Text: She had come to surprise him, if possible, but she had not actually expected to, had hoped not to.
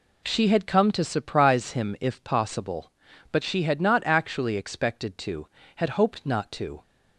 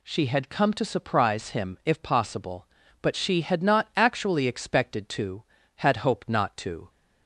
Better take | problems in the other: neither | none

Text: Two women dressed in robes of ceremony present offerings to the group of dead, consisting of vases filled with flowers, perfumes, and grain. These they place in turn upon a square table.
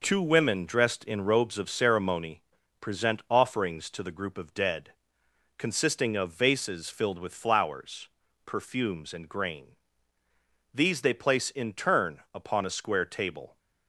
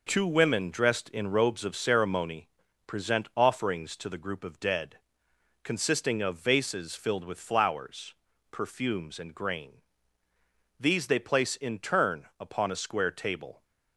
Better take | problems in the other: neither | pauses between "ceremony" and "present"; the same in both

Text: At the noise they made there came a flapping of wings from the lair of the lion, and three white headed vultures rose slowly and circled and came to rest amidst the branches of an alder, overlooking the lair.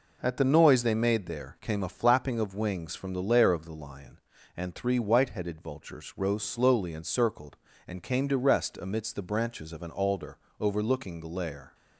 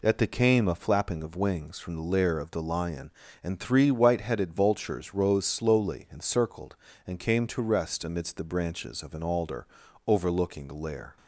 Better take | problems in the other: first | skips "noise they made there"; at 0.2 s

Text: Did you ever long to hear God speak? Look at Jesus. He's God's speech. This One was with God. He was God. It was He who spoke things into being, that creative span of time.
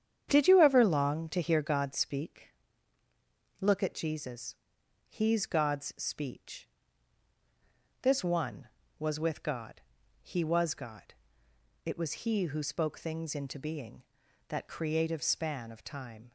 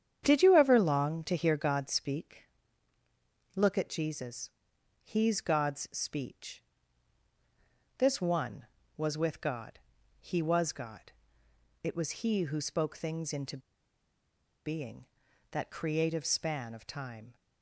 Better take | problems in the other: first | starts louder than the rest; strong; until 1.2 s; 8.5 dB; strong in the first // pauses between "into" and "being"; at 13.5 s; 1.0 s long

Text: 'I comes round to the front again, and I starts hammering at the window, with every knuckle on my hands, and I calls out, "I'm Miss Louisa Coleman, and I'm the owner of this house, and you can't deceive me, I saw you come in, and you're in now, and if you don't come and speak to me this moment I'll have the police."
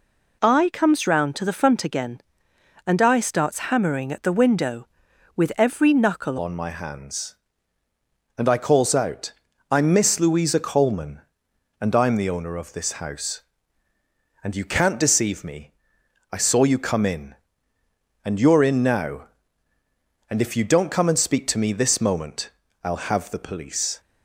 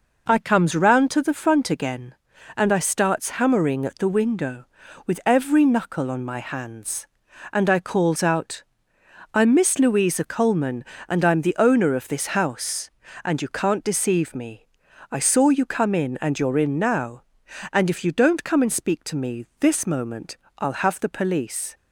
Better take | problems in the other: second | changes voice at "on"; from 6.3 s on; 17.6 s long // pauses between "moment" and "I'll"; slight; at 22.4 s; 0.34 s long; slight in the second

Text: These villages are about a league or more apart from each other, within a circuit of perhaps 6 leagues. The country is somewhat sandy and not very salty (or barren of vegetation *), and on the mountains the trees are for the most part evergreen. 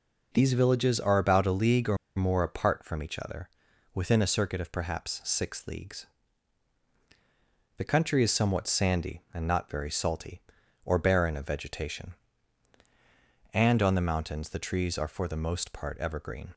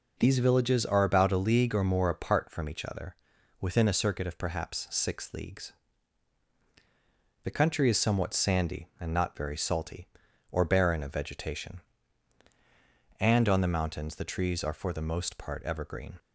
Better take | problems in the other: second | pauses between "or" and "more"; slight; at 1.9 s; 0.20 s long

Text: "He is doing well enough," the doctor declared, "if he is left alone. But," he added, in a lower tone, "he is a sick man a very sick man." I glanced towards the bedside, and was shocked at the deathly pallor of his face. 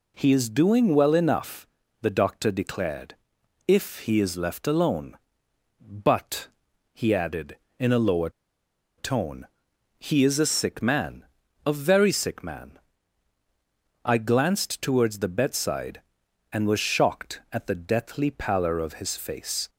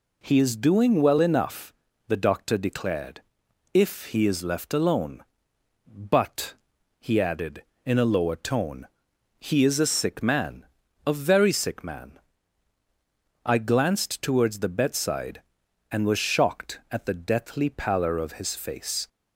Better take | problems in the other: second | pauses between "lower" and "tone"; noticeable; at 8.2 s; 0.68 s long // pauses between "man" and "a"; at 11.2 s; 0.40 s long; also in the second

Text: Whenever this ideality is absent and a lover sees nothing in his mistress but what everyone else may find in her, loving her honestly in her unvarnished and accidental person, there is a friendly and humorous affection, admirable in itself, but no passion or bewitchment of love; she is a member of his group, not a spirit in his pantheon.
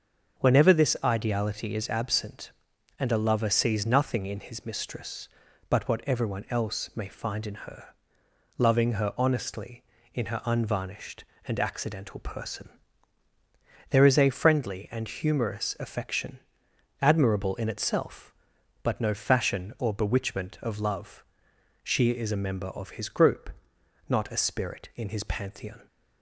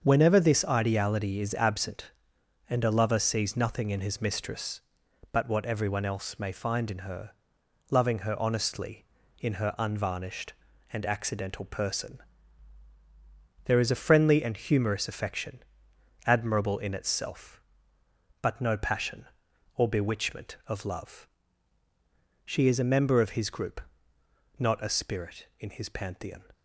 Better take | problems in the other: second | starts louder than the rest; until 1.4 s; 6.5 dB; also in the second // says "fashion" for "passion"; at 19.1 s

